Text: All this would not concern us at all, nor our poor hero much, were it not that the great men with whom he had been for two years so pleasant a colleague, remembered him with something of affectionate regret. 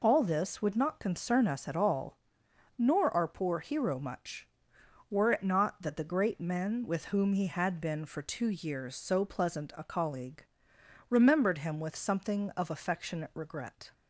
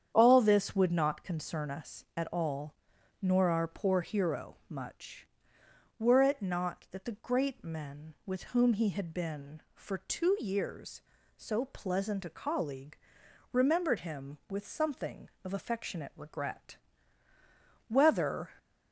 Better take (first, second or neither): first